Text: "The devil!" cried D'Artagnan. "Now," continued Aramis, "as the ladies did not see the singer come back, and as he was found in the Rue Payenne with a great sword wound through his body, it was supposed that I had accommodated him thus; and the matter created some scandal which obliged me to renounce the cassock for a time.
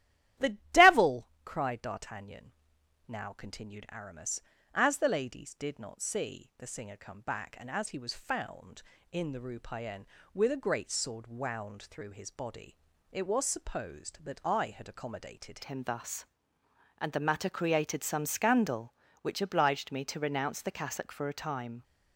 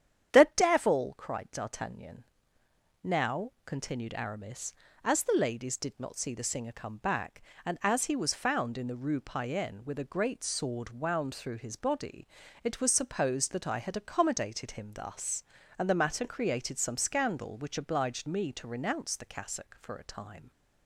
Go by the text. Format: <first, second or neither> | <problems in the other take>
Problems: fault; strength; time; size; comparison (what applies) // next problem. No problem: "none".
second | starts louder than the rest; strong; until 1.7 s; 13 dB; strong in the second // changes voice at "him"; from 15.6 s on; 6.2 s long